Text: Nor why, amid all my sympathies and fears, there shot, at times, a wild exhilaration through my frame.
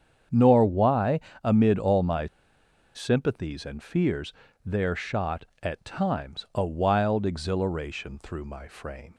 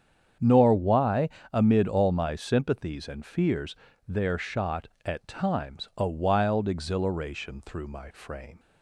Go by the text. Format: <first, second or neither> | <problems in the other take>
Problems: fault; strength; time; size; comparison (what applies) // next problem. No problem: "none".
second | starts louder than the rest; strong; until 1.5 s; 8 dB; strong in the second // pauses between "my" and "sympathies"; noticeable; at 2.2 s; 0.68 s long